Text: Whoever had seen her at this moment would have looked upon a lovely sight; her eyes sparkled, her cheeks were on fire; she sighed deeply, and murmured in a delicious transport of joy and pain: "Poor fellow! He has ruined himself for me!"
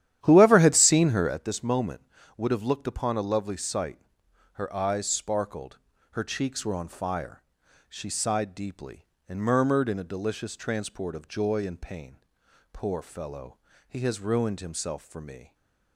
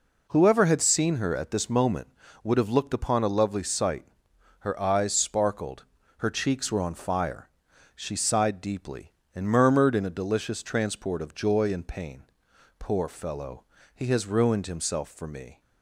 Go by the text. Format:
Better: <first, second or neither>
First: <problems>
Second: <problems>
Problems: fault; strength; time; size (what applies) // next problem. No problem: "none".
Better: second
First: starts louder than the rest; strong; until 1.4 s; 11.5 dB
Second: none